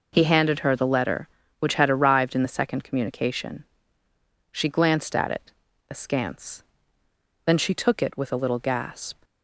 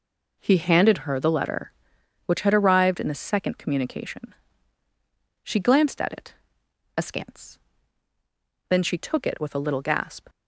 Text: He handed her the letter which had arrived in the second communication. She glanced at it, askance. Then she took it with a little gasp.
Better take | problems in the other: neither | none

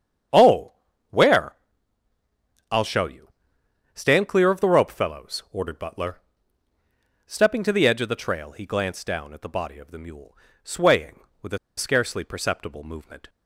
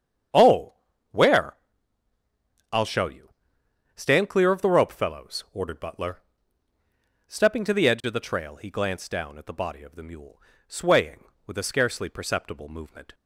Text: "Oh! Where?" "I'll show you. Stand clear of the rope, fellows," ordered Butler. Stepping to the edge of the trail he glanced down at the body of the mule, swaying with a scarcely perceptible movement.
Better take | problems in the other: second | starts louder than the rest; strong; until 2.8 s; 8 dB; strong in the second // pauses between "a" and "scarcely"; slight; at 11.5 s; 0.19 s long

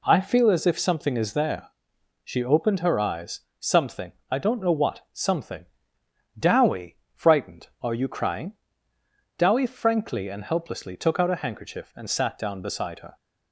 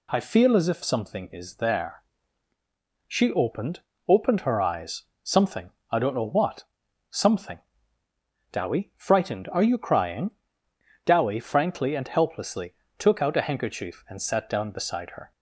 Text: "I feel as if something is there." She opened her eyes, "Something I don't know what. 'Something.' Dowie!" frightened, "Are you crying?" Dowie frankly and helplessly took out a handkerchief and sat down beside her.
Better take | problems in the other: first | says "opened" twice; at 4.0 s // pauses between "Something" and "I"; slight; at 5.6 s; 0.22 s long; slight in the first // pauses between "helplessly" and "took"; slight; at 12.7 s; 0.24 s long

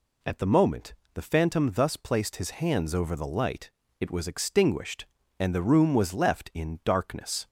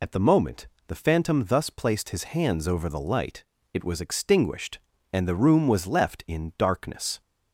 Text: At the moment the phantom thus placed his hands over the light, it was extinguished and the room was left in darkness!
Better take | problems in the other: first | loses the start of "At"; at 0.0 s; 55 ms // pauses between "moment" and "the"; slight; at 0.6 s; 0.22 s long; slight in the first

